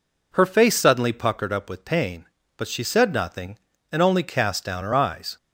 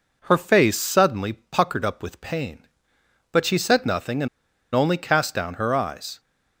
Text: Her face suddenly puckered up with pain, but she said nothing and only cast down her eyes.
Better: first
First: none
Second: pauses between "and" and "only"; noticeable; at 4.2 s; 0.47 s long

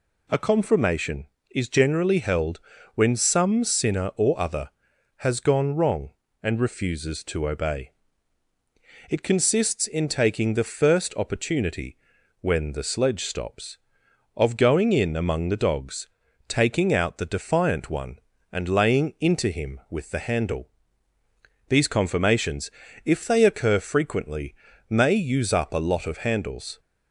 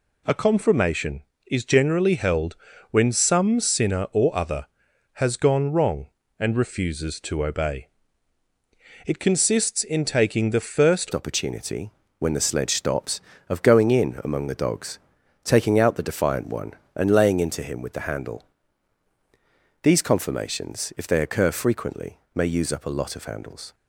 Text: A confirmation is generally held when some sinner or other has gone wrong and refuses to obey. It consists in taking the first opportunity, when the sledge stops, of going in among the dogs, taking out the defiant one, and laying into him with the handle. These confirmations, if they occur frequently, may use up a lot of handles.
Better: first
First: pauses between "held" and "when"; slight; at 2.5 s; 0.36 s long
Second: pauses between "held" and "when"; slight; at 2.5 s; 0.36 s long // changes voice at "opportunity"; from 11.1 s on; 12.6 s long

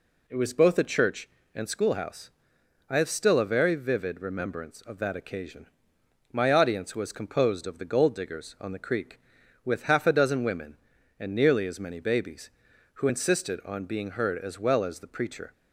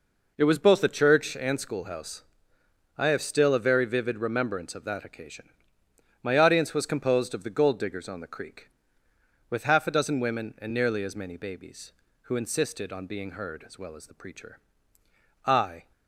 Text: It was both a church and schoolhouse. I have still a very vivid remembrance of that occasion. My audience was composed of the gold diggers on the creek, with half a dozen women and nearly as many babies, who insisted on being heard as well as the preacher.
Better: first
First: none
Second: goes on to say "I"; slight; from 15.4 s on; 0.46 s long

